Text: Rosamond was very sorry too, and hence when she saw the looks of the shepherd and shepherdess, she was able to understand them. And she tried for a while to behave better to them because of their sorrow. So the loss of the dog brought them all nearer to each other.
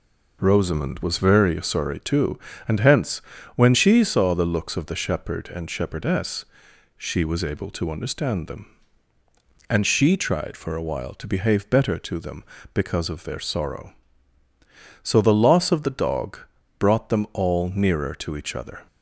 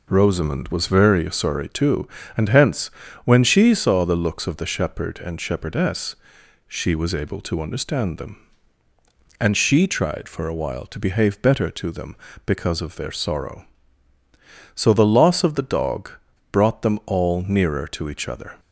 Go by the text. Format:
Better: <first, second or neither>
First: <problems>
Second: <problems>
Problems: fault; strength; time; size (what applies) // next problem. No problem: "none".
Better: neither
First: pauses between "hence" and "when"; at 3.1 s; 0.38 s long // pauses between "dog" and "brought"; at 16.3 s; 0.40 s long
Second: pauses between "hence" and "when"; at 2.8 s; 0.38 s long // pauses between "dog" and "brought"; at 16.1 s; 0.40 s long